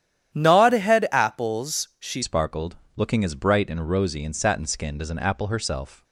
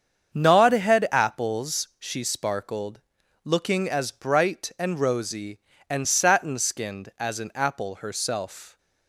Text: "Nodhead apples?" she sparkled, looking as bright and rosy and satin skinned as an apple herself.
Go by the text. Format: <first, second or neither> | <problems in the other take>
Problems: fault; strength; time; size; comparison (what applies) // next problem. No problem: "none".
second | starts louder than the rest; strong; until 1.3 s; 10.5 dB; strong in the second // changes voice at "sparkled"; from 2.2 s on; 3.8 s long